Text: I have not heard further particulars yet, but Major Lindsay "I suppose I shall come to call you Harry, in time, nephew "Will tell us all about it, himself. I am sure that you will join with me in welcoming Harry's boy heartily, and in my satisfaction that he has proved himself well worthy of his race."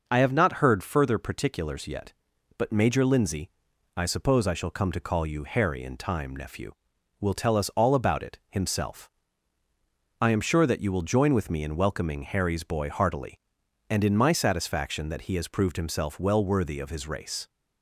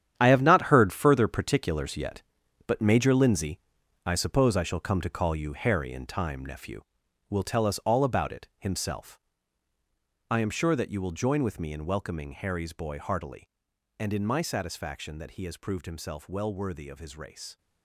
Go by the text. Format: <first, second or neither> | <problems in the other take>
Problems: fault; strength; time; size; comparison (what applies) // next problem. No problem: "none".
first | gets quieter; strong; throughout; 11.5 dB // pauses between "Lindsay" and "I"; noticeable; at 3.5 s; 0.46 s long; noticeable in the first